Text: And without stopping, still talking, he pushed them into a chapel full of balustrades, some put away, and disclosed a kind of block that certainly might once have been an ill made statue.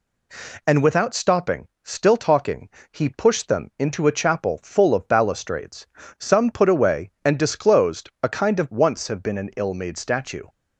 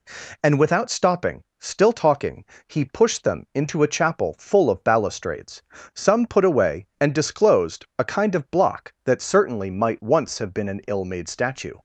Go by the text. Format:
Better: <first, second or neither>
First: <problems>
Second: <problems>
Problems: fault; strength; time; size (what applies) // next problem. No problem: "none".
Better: second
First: skips "block that certainly might"; at 8.7 s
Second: none